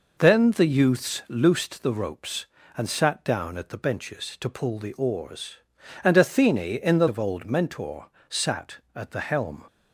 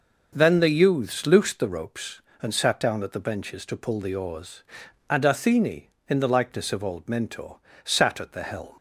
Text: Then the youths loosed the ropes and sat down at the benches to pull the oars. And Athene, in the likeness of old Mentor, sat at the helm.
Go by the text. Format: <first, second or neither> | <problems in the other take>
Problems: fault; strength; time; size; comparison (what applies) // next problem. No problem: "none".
second | skips "likeness"; at 7.0 s